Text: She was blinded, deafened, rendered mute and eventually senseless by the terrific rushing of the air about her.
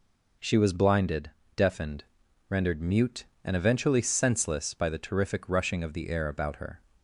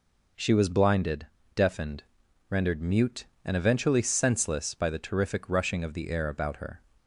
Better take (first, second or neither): neither